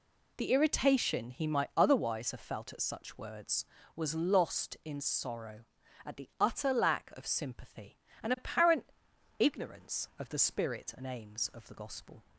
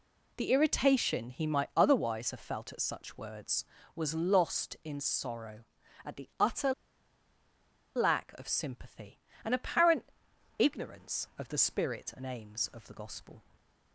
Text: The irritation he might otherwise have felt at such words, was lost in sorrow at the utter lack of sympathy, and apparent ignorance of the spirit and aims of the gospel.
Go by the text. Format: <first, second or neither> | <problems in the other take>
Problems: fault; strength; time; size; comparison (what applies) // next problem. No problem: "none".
first | pauses between "utter" and "lack"; at 6.7 s; 1.2 s long // pauses between "apparent" and "ignorance"; noticeable; at 10.0 s; 0.54 s long; noticeable in the first